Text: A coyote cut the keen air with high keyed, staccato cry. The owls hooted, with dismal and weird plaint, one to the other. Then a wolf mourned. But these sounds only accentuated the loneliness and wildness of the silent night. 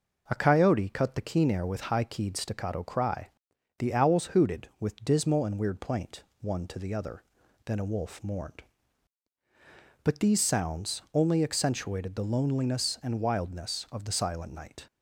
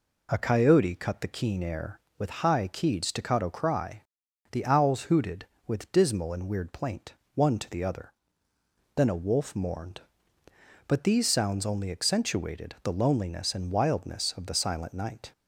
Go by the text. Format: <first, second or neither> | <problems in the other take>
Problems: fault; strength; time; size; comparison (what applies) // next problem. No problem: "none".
neither | none